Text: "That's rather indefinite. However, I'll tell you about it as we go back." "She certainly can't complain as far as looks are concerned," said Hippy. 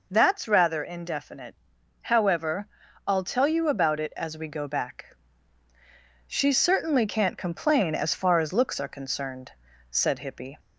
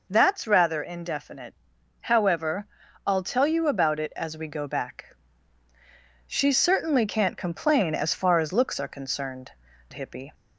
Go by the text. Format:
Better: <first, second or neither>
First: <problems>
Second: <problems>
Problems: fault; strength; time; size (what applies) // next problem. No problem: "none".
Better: first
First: none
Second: skips "said"; at 9.7 s